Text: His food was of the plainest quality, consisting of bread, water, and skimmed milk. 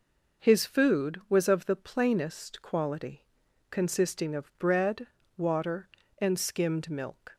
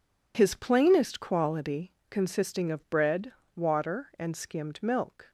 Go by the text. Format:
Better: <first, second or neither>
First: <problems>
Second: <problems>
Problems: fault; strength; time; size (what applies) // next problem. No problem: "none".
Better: first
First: none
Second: skips "food was of the"; at 0.5 s